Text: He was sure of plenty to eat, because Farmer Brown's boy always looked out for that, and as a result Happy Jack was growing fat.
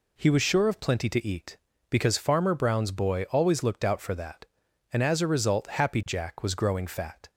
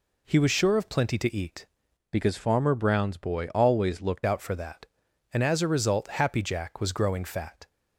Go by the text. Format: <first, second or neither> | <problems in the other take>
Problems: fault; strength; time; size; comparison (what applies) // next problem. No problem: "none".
first | changes voice from "because" to "looked"; from 2.1 to 4.2 s; 2.1 s long